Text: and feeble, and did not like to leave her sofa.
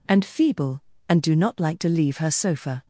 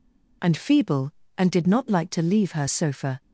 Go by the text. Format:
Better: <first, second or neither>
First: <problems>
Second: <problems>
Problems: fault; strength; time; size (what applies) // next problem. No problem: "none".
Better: second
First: says "do" for "did"; at 1.2 s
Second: none